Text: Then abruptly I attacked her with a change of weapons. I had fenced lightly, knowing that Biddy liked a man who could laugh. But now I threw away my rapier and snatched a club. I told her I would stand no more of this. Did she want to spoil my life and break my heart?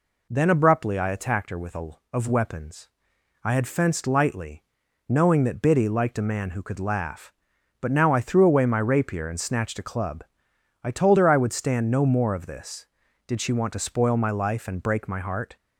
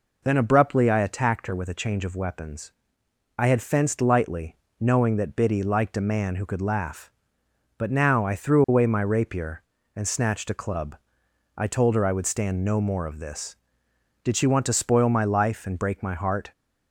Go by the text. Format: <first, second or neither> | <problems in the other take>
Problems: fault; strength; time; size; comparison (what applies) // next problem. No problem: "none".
second | skips "change"; at 2.0 s